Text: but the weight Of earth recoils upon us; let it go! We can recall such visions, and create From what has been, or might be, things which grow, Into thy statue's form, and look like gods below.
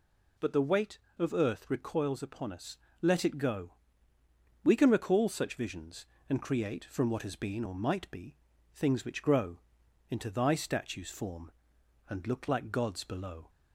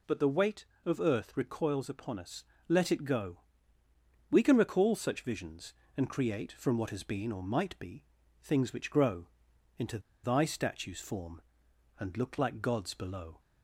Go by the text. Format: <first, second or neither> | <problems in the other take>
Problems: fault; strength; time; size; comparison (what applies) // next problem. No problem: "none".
first | pauses between "Into" and "thy"; slight; at 9.9 s; 0.24 s long